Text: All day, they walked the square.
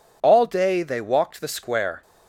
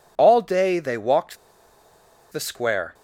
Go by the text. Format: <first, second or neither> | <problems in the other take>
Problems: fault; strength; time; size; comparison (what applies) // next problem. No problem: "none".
first | pauses between "walked" and "the"; noticeable; at 1.3 s; 0.94 s long